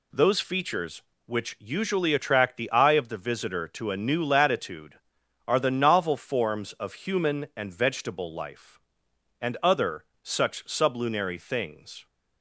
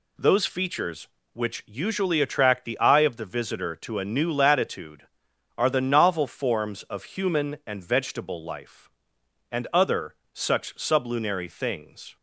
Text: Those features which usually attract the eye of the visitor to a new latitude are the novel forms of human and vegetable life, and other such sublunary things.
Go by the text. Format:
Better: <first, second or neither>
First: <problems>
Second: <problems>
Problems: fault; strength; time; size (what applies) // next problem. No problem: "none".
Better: neither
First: pauses between "other" and "such"; slight; at 10.0 s; 0.18 s long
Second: pauses between "other" and "such"; slight; at 10.1 s; 0.18 s long